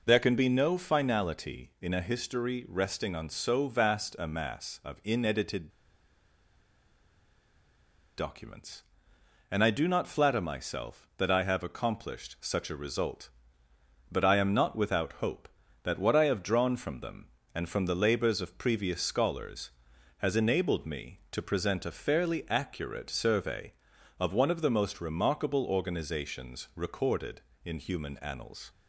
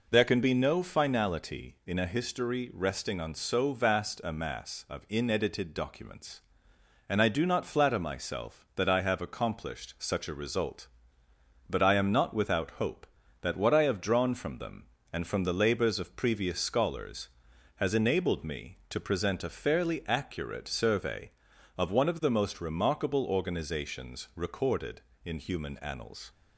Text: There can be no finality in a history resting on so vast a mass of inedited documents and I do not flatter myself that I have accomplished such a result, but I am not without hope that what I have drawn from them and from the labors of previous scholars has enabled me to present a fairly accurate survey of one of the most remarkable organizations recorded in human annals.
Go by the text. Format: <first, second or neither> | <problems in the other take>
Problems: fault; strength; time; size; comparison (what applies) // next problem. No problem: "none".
second | pauses between "inedited" and "documents"; strong; at 5.6 s; 2.4 s long